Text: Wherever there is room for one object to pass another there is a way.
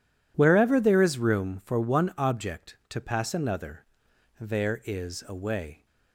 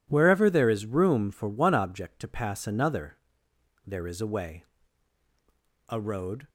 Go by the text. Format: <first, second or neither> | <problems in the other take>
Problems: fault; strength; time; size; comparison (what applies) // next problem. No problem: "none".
first | pauses between "another" and "there"; noticeable; at 3.1 s; 0.68 s long; noticeable in the first // goes on to say "A road"; from 5.8 s on; 0.60 s long